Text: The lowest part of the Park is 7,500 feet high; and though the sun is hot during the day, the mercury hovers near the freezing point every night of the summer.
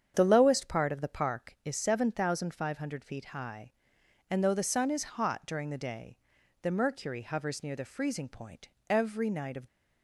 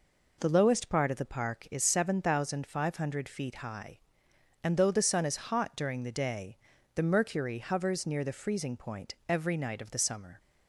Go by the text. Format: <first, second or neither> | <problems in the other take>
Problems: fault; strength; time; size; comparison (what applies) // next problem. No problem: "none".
second | starts louder than the rest; strong; until 1.1 s; 8 dB // pauses between "point" and "every"; slight; at 8.6 s; 0.20 s long // stops before "the summer"; at 9.6 s